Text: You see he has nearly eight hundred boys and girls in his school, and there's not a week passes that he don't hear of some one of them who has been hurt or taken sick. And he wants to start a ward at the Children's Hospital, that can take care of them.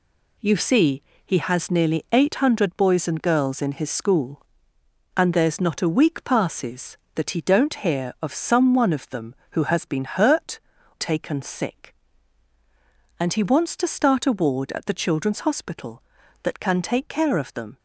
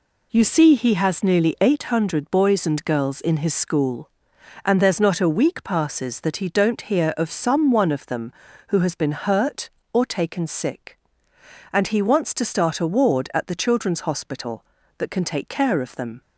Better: second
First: pauses between "see" and "he"; slight; at 1.0 s; 0.24 s long // skips "or"; at 10.7 s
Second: none

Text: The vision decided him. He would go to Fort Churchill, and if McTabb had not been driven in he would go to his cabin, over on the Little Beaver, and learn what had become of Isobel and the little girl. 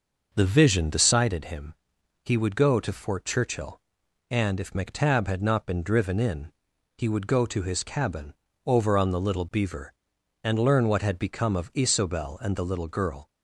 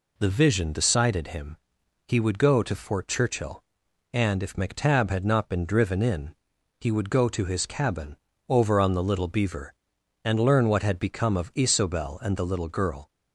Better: second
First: starts louder than the rest; noticeable; until 1.2 s; 6 dB // pauses between "in" and "he"; noticeable; at 6.5 s; 0.46 s long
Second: pauses between "in" and "he"; noticeable; at 6.3 s; 0.46 s long

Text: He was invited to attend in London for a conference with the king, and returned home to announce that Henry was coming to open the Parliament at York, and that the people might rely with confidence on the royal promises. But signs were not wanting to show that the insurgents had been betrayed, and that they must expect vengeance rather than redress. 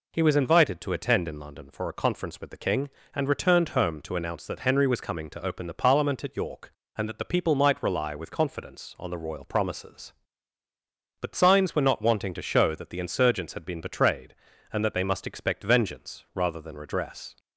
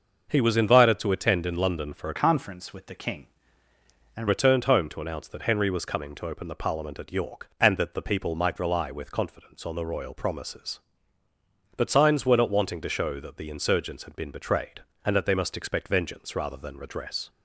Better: first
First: none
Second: starts louder than the rest; noticeable; until 1.3 s; 6 dB // changes voice from "conference" to "and"; from 2.1 to 4.2 s; 2.1 s long

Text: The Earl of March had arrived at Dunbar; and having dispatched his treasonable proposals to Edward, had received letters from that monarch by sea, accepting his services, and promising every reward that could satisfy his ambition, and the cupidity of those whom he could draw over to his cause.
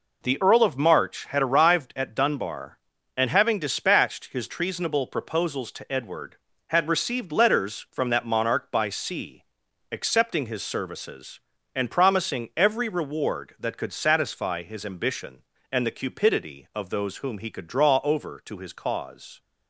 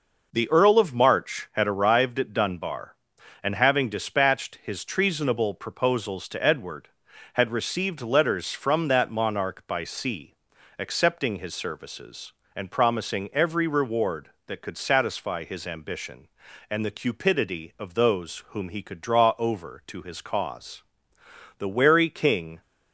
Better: first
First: none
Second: goes on to say "The wary king"; noticeable; from 21.5 s on; 1.0 s long

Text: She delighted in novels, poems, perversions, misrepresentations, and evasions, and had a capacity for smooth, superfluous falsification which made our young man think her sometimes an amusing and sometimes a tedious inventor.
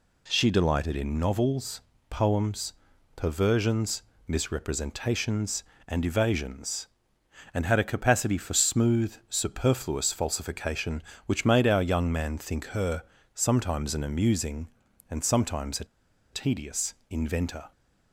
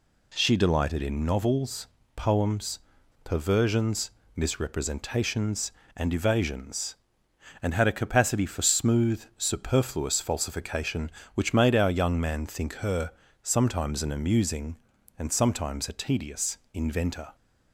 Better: second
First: pauses between "her" and "sometimes"; slight; at 13.0 s; 0.32 s long // pauses between "a" and "tedious"; noticeable; at 15.8 s; 0.47 s long // pauses between "tedious" and "inventor"; slight; at 16.9 s; 0.16 s long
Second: pauses between "her" and "sometimes"; slight; at 13.1 s; 0.32 s long // pauses between "tedious" and "inventor"; slight; at 16.5 s; 0.16 s long

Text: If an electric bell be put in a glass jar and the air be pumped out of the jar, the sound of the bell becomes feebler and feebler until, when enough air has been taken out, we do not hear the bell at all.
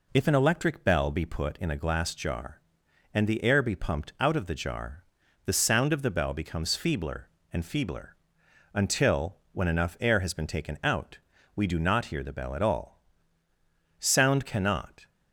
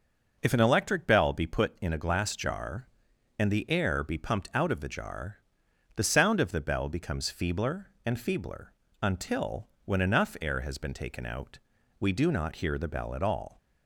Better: second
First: pauses between "feebler" and "until"; noticeable; at 8.1 s; 0.58 s long // goes on to say "Sound cannot"; noticeable; from 13.9 s on; 1.1 s long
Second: pauses between "feebler" and "until"; slight; at 8.7 s; 0.30 s long

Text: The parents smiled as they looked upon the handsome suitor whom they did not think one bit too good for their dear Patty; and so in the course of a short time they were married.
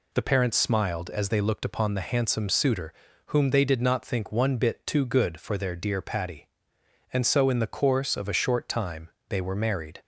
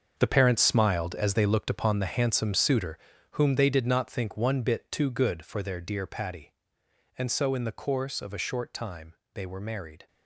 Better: first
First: pauses between "suitor" and "whom"; slight; at 2.9 s; 0.34 s long // pauses between "time" and "they"; slight; at 9.0 s; 0.22 s long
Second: gets quieter; strong; throughout; 12 dB // pauses between "suitor" and "whom"; slight; at 2.9 s; 0.34 s long // pauses between "time" and "they"; slight; at 9.1 s; 0.22 s long

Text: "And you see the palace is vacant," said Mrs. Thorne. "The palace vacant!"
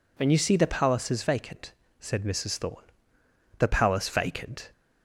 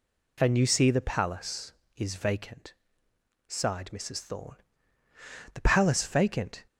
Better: first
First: none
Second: says "sighed" for "said"; at 3.4 s

